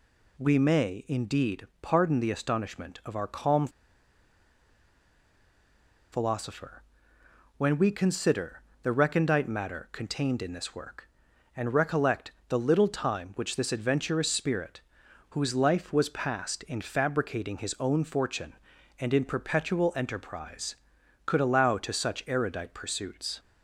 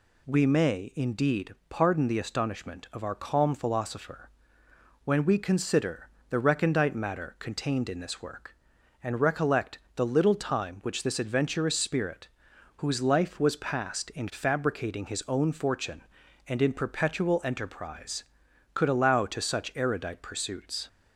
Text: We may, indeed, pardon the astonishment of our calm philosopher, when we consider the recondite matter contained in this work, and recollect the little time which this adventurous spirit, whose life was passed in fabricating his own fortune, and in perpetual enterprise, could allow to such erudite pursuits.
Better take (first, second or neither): second